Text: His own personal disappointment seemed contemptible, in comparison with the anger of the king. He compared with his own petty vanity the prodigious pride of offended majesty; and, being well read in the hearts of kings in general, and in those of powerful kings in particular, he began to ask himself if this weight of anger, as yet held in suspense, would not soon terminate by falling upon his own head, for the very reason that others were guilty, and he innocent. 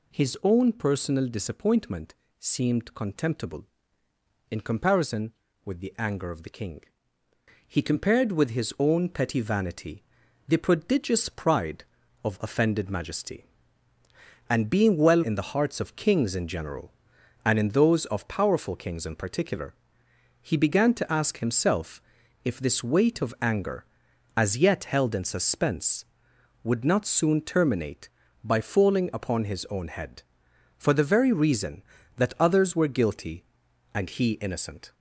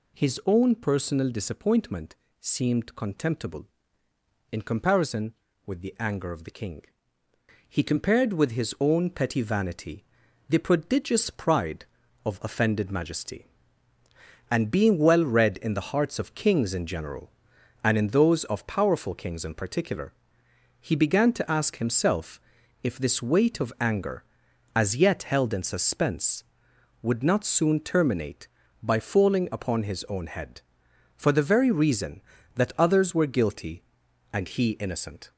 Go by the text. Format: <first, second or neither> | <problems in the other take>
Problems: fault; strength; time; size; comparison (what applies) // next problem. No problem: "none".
second | pauses between "disappointment" and "seemed"; slight; at 2.1 s; 0.22 s long; slight in the second // pauses between "vanity" and "the"; noticeable; at 10.0 s; 0.46 s long; noticeable in the second // skips "read"; at 15.2 s // pauses between "himself" and "if"; at 21.9 s; 0.44 s long; also in the second